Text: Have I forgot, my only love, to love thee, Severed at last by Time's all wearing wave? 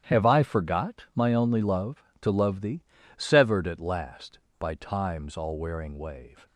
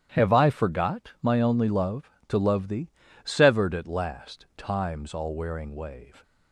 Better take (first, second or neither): first